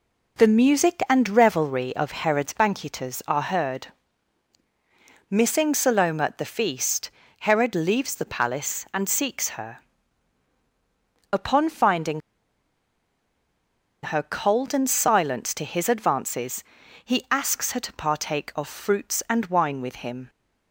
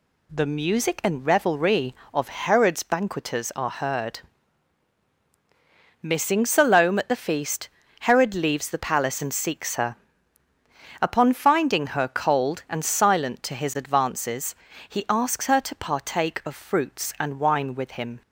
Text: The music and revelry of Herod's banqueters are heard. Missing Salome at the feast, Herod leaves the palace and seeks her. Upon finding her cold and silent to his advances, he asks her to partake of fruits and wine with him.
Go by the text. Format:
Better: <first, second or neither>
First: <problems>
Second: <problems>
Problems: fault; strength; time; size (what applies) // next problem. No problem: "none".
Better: second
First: pauses between "finding" and "her"; strong; at 12.1 s; 1.9 s long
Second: none